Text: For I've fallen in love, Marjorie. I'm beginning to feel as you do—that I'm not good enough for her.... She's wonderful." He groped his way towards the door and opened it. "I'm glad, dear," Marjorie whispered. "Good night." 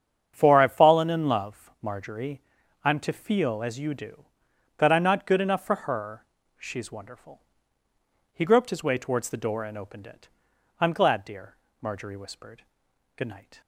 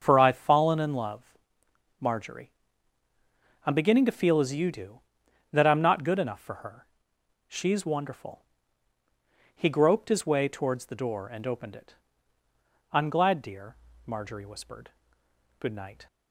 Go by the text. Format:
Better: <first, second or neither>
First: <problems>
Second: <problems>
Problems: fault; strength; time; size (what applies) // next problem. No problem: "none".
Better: second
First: starts louder than the rest; strong; until 1.3 s; 8 dB // skips "beginning"; at 2.9 s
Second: starts louder than the rest; until 1.0 s; 6.5 dB